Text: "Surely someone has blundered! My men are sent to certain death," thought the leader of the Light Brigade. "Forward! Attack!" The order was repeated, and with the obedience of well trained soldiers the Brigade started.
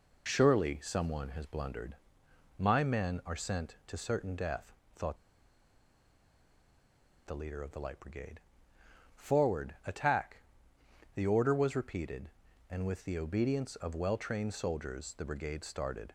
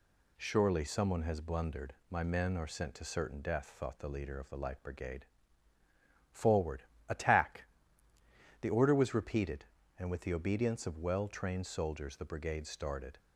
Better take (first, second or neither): second